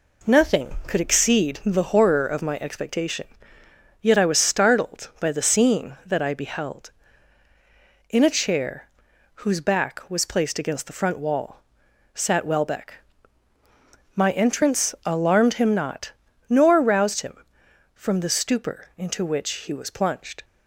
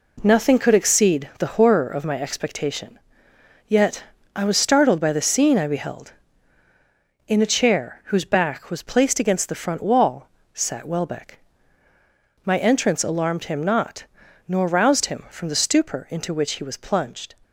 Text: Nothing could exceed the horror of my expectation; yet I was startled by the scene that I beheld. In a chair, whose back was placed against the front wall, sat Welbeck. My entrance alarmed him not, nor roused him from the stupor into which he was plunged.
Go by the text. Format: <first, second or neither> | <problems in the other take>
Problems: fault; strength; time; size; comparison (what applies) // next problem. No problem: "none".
first | pauses between "yet" and "I"; slight; at 4.0 s; 0.32 s long // skips "that"; at 5.5 s